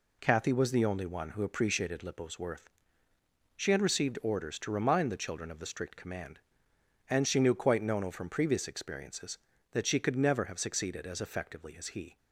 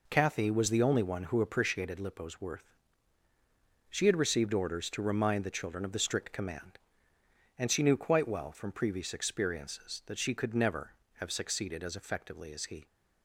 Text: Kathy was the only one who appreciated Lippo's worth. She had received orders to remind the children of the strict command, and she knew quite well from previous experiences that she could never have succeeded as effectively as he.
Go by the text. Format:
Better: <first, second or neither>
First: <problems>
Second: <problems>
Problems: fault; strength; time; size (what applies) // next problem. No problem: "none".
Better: second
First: says "nono" for "well"; at 7.8 s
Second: none